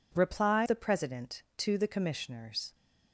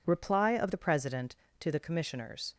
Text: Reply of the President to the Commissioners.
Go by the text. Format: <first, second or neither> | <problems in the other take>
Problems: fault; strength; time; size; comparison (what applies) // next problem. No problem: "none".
second | skips "of"; at 0.6 s